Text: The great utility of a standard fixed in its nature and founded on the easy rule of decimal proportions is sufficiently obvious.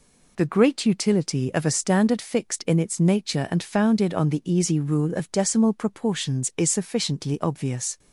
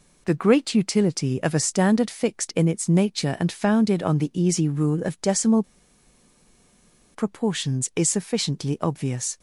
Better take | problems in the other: first | pauses between "decimal" and "proportions"; strong; at 5.6 s; 1.5 s long

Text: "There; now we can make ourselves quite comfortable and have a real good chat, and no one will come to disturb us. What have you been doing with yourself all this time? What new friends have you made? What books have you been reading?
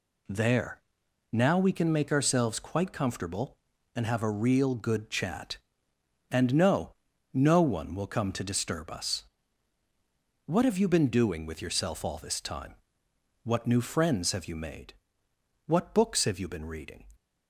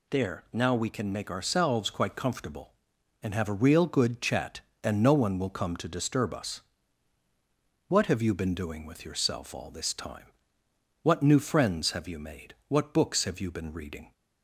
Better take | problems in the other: second | says "no" twice; at 7.3 s

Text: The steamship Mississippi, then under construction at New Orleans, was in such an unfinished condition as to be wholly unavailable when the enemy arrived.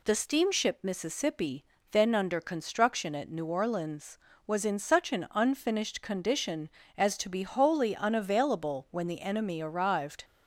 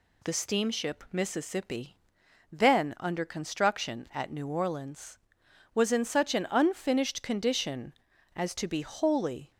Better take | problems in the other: first | stops before "unavailable when the enemy arrived"; at 9.5 s

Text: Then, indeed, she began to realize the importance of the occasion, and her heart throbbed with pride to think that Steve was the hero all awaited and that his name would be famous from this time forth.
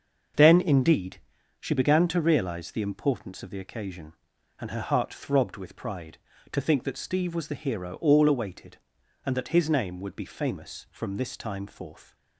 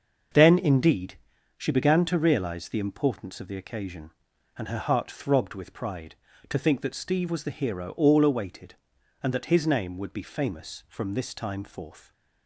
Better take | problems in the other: neither | starts louder than the rest; the same in both

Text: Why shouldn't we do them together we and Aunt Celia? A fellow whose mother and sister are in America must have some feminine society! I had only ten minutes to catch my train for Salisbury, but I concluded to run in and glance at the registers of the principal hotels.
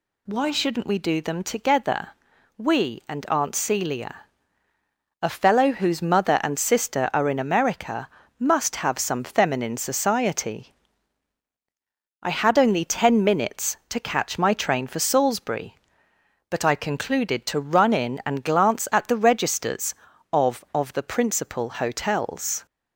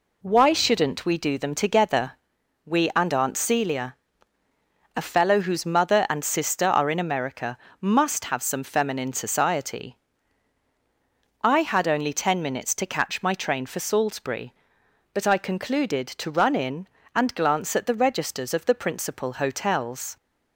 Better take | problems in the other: second | pauses between "together" and "we"; noticeable; at 2.0 s; 0.48 s long; noticeable in the second // pauses between "America" and "must"; slight; at 8.0 s; 0.32 s long; slight in the second // says "of" twice; at 20.7 s

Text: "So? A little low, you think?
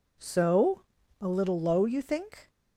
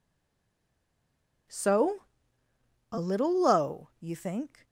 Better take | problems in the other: first | stays silent before the first word; noticeable; until 1.4 s; 1.4 s long

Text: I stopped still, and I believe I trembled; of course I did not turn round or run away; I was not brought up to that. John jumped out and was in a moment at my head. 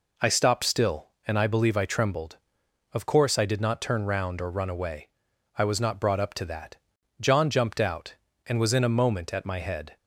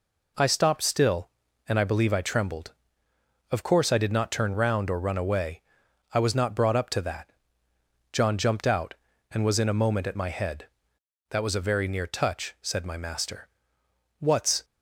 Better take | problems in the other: first | goes on to say "That was a very near touch said my master What's"; strong; from 11.2 s on; 3.3 s long

